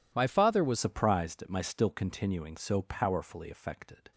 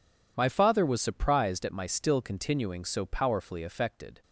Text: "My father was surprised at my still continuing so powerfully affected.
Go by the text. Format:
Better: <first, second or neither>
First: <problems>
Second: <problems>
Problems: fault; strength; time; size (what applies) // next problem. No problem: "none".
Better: second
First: changes voice at "surprised"; from 0.7 s on; 3.4 s long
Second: none